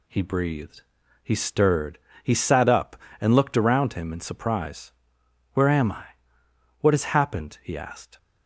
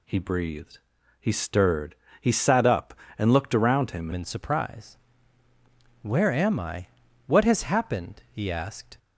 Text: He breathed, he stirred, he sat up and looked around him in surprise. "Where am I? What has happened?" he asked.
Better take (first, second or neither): first